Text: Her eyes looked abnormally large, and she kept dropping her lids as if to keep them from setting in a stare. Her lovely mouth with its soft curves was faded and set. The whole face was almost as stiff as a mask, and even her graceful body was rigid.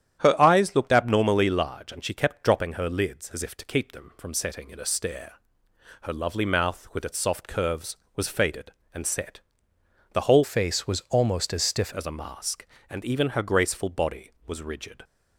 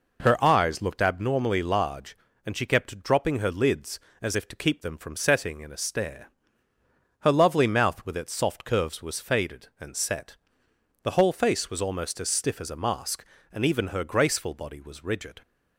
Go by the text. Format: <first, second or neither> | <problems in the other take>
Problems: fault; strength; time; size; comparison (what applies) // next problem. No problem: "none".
second | starts louder than the rest; strong; until 1.2 s; 10 dB // changes voice from "face" to "stiff"; from 10.4 to 11.9 s; 1.5 s long